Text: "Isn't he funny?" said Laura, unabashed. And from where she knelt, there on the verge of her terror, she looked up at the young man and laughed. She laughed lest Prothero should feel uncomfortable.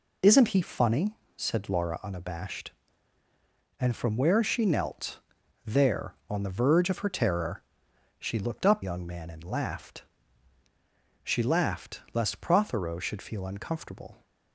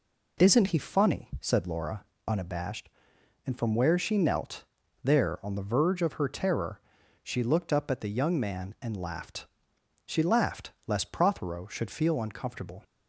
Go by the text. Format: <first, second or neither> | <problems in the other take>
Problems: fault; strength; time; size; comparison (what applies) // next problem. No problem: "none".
second | skips "at the"; at 8.8 s